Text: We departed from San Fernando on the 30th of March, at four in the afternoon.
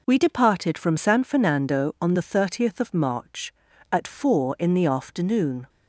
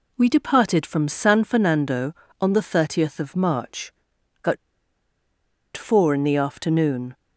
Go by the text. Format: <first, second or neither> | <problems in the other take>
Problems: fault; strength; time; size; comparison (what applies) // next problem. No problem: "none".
first | pauses between "at" and "four"; at 4.5 s; 1.1 s long